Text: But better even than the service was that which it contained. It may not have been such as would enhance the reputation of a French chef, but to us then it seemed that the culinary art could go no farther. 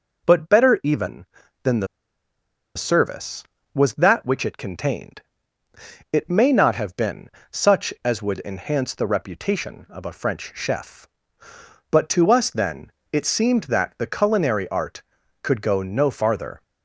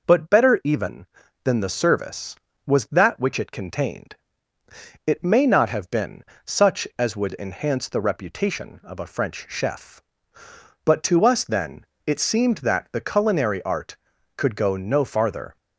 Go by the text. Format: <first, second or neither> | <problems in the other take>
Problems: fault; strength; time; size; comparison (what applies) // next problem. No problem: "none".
second | pauses between "the" and "service"; noticeable; at 1.8 s; 0.91 s long // pauses between "been" and "such"; slight; at 7.2 s; 0.22 s long; slight in the second // pauses between "then" and "it"; slight; at 12.9 s; 0.20 s long; slight in the second